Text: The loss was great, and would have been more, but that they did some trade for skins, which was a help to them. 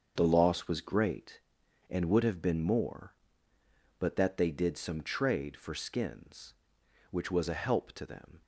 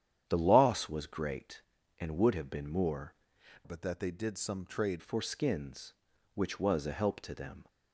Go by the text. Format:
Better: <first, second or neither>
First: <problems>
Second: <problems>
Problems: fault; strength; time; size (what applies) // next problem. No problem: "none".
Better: first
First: starts louder than the rest; until 1.1 s; 7 dB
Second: starts louder than the rest; strong; until 1.2 s; 9.5 dB // changes voice from "but" to "trade"; from 3.6 to 5.0 s; 1.4 s long